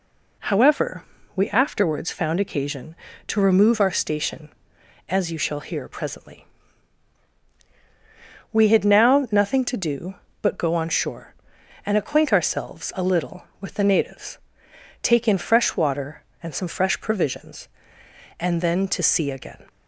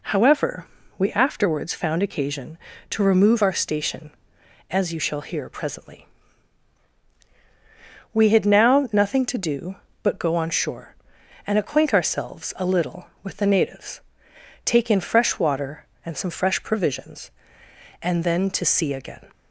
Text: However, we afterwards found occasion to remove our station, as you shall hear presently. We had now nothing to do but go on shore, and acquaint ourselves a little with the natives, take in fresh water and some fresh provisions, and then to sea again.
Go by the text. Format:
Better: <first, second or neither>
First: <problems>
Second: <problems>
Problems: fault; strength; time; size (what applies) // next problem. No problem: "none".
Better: neither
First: none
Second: none